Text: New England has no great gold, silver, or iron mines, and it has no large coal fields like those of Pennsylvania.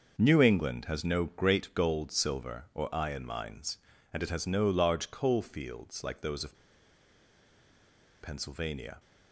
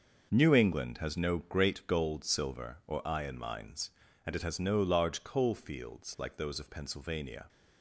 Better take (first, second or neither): second